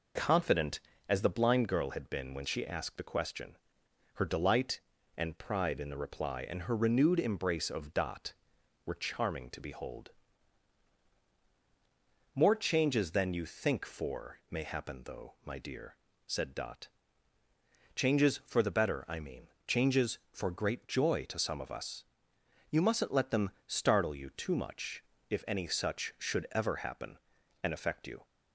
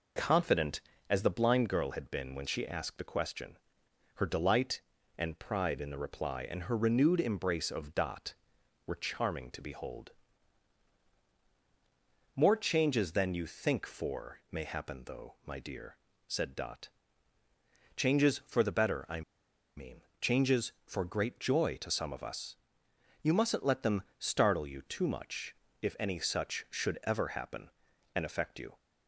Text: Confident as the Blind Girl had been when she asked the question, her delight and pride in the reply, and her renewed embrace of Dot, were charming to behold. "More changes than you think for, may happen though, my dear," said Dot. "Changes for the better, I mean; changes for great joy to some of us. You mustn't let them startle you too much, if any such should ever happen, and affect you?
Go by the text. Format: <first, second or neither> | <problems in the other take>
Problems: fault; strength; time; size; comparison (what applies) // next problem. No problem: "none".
first | pauses between "I" and "mean"; noticeable; at 19.2 s; 0.55 s long // pauses between "them" and "startle"; slight; at 24.0 s; 0.16 s long; slight in the first